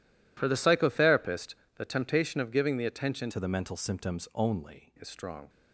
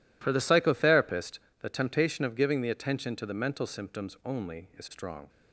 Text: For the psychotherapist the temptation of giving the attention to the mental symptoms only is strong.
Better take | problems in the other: second | pauses between "psychotherapist" and "the"; slight; at 1.5 s; 0.22 s long; slight in the second // changes voice from "to" to "only"; from 3.2 to 4.9 s; 1.7 s long

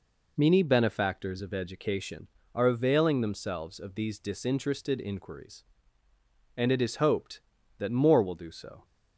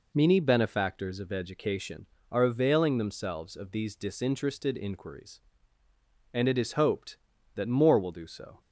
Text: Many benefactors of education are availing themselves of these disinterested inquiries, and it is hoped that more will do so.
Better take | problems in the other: neither | none

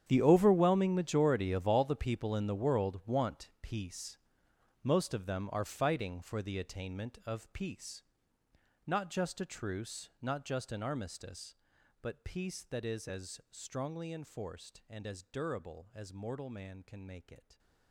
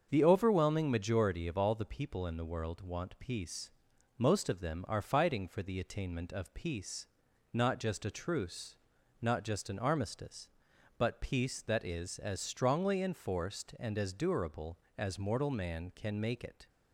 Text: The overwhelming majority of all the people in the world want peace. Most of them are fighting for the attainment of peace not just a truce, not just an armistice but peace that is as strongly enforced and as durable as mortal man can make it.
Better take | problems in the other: second | gets quieter; strong; throughout; 17.5 dB // starts louder than the rest; strong; until 1.0 s; 9 dB; also in the second // pauses between "peace" and "not"; noticeable; at 8.0 s; 0.86 s long; also in the second

